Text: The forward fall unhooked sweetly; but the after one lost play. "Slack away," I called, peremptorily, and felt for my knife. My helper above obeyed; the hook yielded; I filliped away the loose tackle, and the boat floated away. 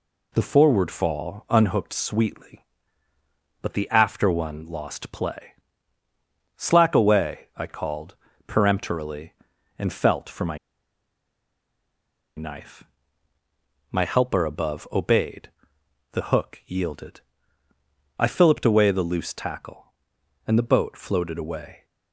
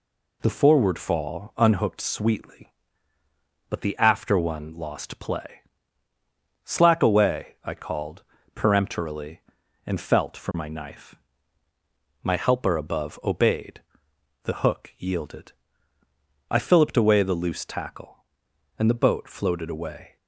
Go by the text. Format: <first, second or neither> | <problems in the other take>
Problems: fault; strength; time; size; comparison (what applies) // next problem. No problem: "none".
second | pauses between "my" and "knife"; strong; at 10.5 s; 1.8 s long